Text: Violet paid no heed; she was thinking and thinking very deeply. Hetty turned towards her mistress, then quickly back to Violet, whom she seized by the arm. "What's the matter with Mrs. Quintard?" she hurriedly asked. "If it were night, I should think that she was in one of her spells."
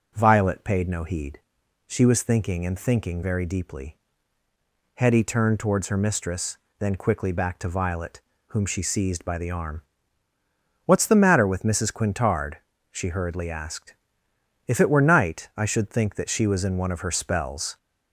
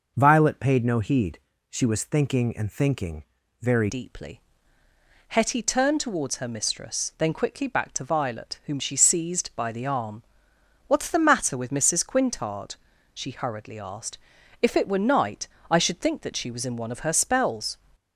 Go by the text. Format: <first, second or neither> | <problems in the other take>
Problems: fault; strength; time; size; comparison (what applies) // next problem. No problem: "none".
first | pauses between "thinking" and "very"; at 3.2 s; 0.38 s long // changes voice at "deeply"; from 3.8 s on; 13.9 s long